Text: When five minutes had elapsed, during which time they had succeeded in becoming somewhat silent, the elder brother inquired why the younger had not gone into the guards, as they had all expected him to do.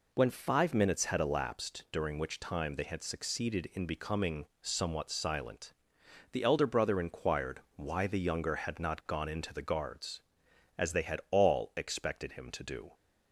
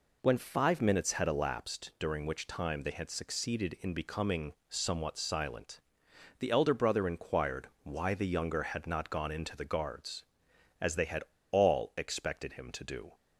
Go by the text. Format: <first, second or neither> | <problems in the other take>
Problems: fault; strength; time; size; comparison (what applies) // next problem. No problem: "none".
first | pauses between "becoming" and "somewhat"; slight; at 4.5 s; 0.16 s long; slight in the first // pauses between "had" and "all"; slight; at 11.2 s; 0.27 s long